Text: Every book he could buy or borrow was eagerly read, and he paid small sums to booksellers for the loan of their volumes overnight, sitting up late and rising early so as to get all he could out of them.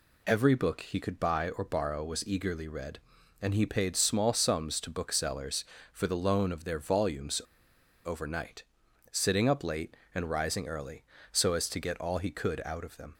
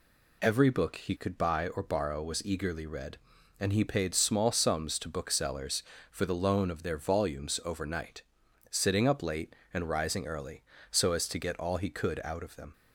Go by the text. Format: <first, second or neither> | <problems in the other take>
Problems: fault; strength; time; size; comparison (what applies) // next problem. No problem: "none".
second | pauses between "volumes" and "overnight"; noticeable; at 7.4 s; 0.63 s long